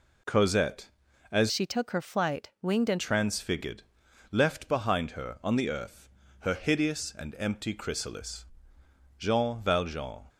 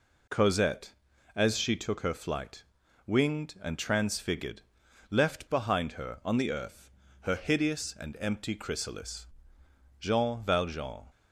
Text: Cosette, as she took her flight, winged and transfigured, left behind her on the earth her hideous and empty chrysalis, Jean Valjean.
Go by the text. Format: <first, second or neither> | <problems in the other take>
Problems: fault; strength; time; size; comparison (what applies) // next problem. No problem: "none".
second | changes voice from "she" to "and"; from 1.5 to 2.9 s; 1.4 s long // pauses between "earth" and "her"; slight; at 6.0 s; 0.32 s long; slight in the second